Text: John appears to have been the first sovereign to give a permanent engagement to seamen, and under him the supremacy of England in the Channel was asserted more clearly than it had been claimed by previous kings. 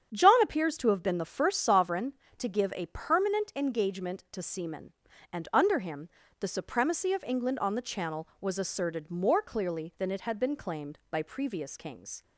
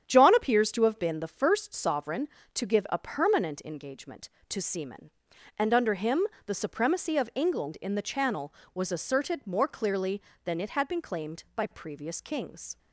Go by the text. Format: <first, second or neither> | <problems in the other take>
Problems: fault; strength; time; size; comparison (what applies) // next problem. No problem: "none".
second | starts louder than the rest; strong; until 1.1 s; 8 dB; strong in the second // pauses between "him" and "the"; slight; at 6.0 s; 0.32 s long; slight in the second // says "on" for "in"; at 7.5 s